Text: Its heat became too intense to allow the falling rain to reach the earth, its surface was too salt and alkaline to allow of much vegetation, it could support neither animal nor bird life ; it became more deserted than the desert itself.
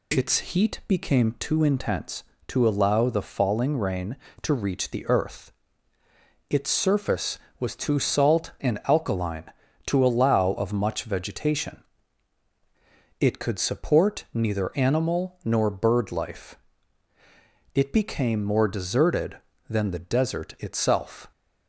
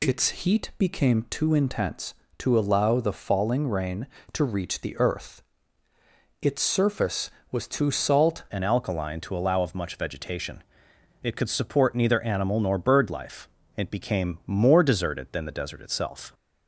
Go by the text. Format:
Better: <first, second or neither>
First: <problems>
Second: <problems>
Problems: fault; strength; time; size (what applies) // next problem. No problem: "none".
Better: first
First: none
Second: changes voice at "and"; from 8.4 s on; 7.9 s long